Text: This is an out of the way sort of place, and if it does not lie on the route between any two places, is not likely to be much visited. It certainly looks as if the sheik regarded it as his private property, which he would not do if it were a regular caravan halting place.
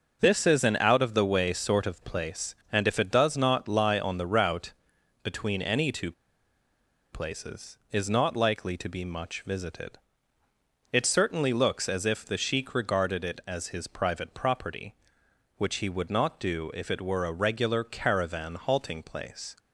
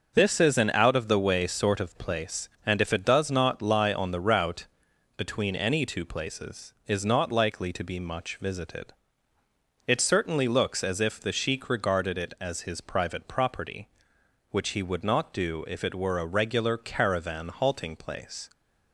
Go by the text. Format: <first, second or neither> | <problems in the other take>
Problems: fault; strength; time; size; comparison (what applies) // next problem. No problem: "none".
second | starts louder than the rest; noticeable; until 1.2 s; 6 dB; noticeable in the second // pauses between "route" and "between"; noticeable; at 4.7 s; 0.50 s long; noticeable in the second // pauses between "two" and "places"; at 6.1 s; 1.0 s long